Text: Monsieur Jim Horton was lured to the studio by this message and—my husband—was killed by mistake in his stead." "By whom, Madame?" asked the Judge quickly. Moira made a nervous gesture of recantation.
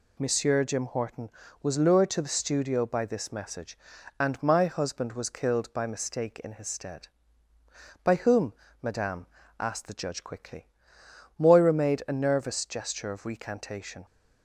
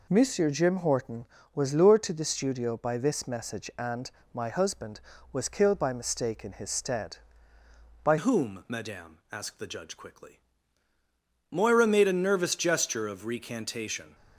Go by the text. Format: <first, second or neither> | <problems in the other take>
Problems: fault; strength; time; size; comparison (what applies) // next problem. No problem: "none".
first | changes voice at "whom"; from 8.1 s on; 6.0 s long